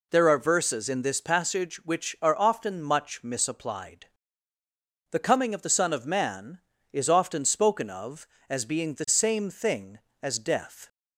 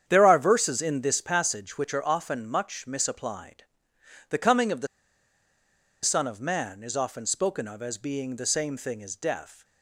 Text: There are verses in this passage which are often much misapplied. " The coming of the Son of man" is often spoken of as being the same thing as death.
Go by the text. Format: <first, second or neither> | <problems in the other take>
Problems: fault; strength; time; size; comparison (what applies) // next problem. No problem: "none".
first | starts louder than the rest; strong; until 1.0 s; 9 dB // pauses between "the" and "Son"; at 4.8 s; 1.1 s long